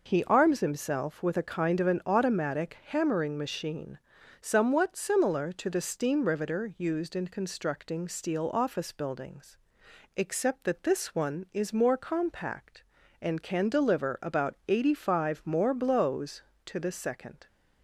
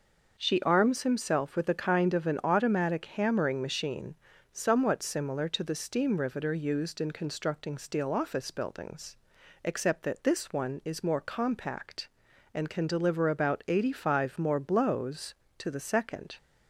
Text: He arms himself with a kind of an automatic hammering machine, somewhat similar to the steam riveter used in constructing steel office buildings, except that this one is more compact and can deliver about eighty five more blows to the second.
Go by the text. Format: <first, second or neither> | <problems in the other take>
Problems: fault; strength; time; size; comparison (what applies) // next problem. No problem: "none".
first | says "She" for "He"; at 0.3 s